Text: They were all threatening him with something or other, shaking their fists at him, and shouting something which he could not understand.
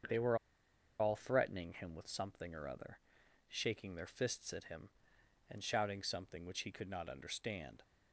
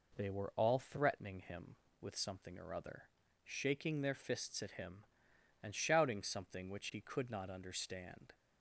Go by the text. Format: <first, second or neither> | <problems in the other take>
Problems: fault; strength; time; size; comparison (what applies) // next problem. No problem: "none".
second | starts louder than the rest; until 1.7 s; 7 dB // pauses between "were" and "all"; noticeable; at 0.3 s; 0.63 s long